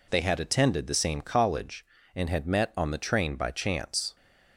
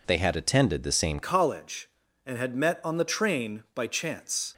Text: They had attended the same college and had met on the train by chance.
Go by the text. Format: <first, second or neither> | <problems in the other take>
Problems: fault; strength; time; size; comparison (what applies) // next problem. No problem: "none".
first | changes voice at "college"; from 1.2 s on; 3.2 s long